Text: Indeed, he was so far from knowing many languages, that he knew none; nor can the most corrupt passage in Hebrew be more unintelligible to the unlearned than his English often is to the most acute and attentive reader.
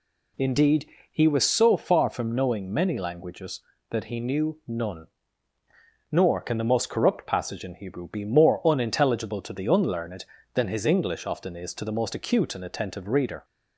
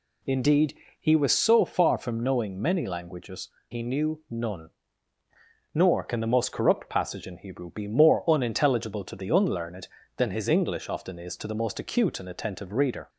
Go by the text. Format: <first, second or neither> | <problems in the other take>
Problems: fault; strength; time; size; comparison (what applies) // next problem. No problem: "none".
first | skips "that"; at 3.5 s